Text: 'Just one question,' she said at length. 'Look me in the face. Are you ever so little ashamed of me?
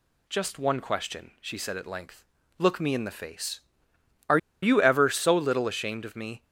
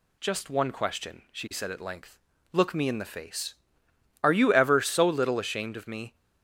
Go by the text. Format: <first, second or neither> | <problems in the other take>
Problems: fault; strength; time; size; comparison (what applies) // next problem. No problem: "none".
second | pauses between "Are" and "you"; slight; at 4.3 s; 0.23 s long